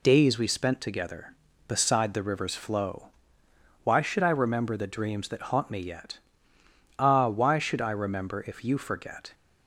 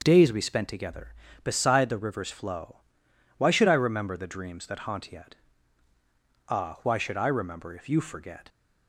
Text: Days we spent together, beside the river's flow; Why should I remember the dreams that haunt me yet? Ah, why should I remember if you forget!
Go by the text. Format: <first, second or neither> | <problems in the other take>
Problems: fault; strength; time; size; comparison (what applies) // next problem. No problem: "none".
first | starts louder than the rest; until 1.0 s; 6 dB // skips "me"; at 5.1 s